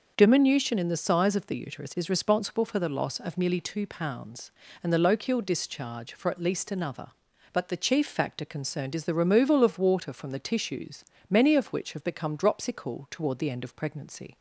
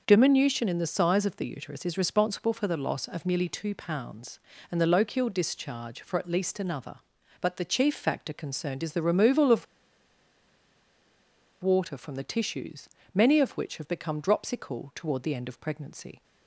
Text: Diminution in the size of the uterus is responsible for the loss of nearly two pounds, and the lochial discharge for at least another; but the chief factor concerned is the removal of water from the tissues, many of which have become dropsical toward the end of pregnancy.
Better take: first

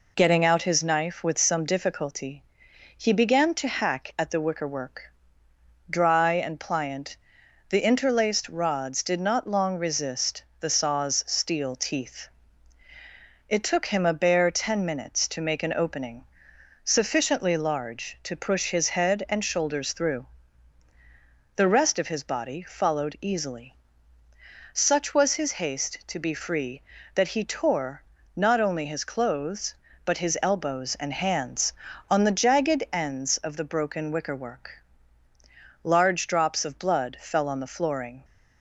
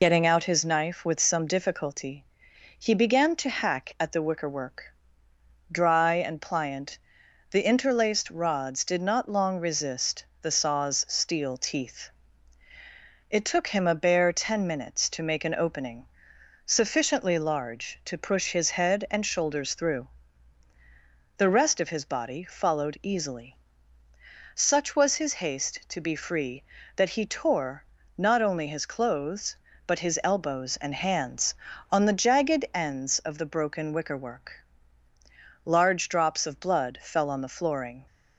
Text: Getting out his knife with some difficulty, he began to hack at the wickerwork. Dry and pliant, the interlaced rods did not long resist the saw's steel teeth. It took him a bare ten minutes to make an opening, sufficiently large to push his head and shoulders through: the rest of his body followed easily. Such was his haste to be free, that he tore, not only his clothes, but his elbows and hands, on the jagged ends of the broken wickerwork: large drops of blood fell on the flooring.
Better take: first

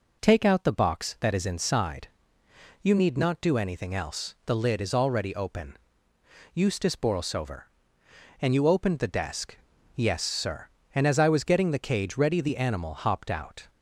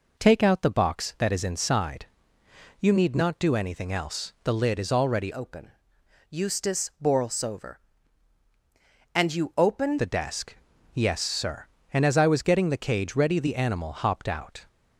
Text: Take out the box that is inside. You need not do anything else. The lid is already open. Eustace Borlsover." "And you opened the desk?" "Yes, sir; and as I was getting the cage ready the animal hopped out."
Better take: first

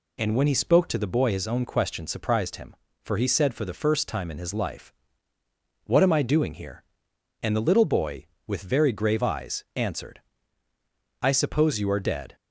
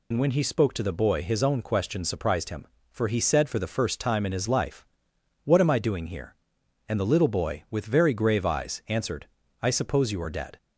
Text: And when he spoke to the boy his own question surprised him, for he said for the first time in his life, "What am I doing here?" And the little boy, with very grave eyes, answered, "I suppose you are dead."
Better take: first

